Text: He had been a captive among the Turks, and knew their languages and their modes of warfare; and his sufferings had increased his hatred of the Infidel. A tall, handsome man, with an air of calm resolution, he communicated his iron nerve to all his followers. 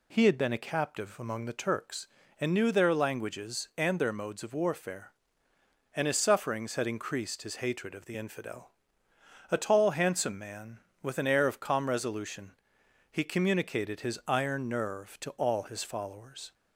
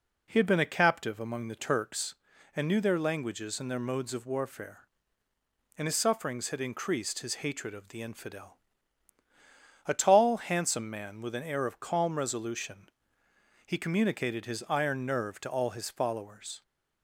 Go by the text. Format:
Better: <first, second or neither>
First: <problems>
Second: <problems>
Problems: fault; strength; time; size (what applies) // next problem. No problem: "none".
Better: neither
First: none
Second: none